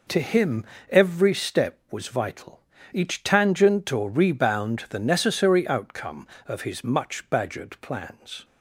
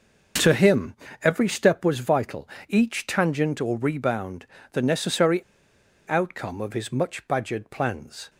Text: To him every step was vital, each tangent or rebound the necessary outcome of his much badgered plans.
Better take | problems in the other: first | starts louder than the rest; noticeable; until 1.6 s; 6 dB // pauses between "him" and "every"; slight; at 0.9 s; 0.28 s long; slight in the first // pauses between "rebound" and "the"; slight; at 4.4 s; 0.26 s long // pauses between "necessary" and "outcome"; noticeable; at 5.4 s; 0.64 s long

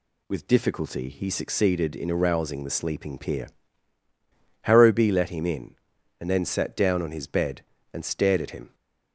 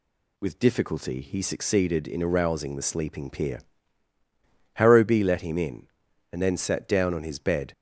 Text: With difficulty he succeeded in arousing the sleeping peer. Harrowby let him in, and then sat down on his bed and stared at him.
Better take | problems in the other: first | stops before "and stared at him"; at 7.7 s

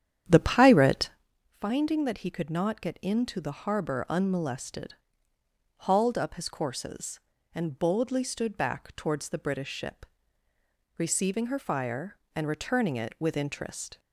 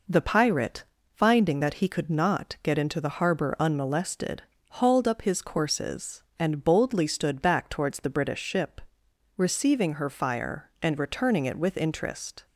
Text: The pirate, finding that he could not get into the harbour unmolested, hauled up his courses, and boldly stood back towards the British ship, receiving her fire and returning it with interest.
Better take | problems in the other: second | starts louder than the rest; strong; until 1.3 s; 9.5 dB

